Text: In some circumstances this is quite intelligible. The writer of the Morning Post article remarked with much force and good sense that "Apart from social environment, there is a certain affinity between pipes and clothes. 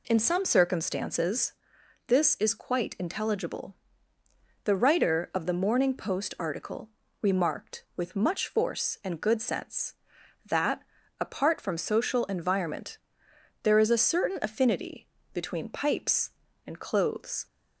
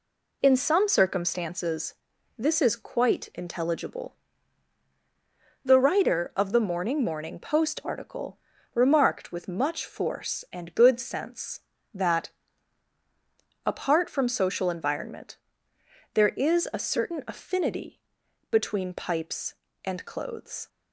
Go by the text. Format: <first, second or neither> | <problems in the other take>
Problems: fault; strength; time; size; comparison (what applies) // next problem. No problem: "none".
first | pauses between "circumstances" and "this"; at 1.9 s; 0.44 s long; noticeable in the first // says "Morning" twice; at 7.0 s // pauses between "article" and "remarked"; slight; at 8.3 s; 0.36 s long; slight in the first // pauses between "that" and "Apart"; strong; at 12.2 s; 1.3 s long; also in the first // pauses between "affinity" and "between"; noticeable; at 17.9 s; 0.50 s long; slight in the first